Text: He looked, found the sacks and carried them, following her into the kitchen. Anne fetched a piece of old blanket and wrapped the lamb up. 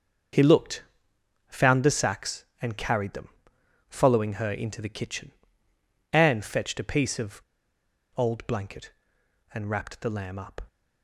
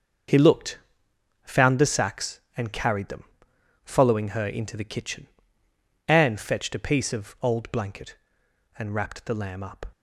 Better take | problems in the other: second | starts louder than the rest; until 2.0 s; 6.5 dB; also in the second // pauses between "of" and "old"; noticeable; at 7.3 s; 0.76 s long

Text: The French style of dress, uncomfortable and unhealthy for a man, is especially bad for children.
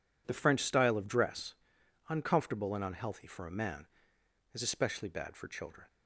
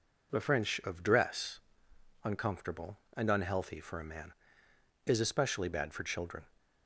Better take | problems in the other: first | skips "style"; at 0.8 s

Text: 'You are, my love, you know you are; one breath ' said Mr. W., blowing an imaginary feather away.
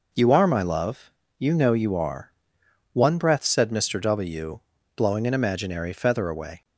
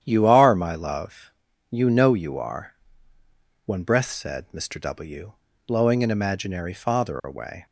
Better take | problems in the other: first | starts louder than the rest; strong; until 1.0 s; 9.5 dB // says "father" for "feather"; at 6.7 s

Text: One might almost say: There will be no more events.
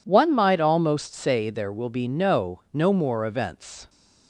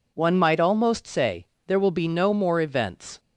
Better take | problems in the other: second | says "no" twice; at 2.7 s

